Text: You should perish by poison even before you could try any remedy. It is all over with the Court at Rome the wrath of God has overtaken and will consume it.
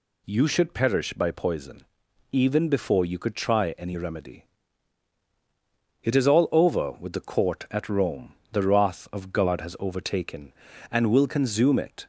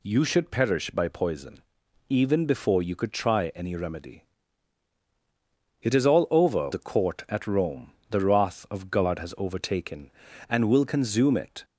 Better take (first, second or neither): first